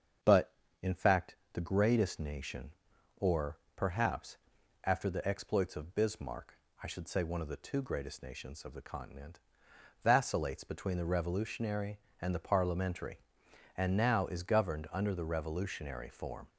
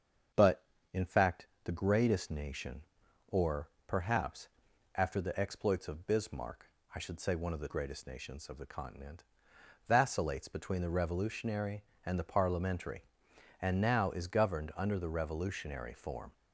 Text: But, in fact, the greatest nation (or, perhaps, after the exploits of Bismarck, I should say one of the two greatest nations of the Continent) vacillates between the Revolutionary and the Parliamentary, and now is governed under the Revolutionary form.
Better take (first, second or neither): first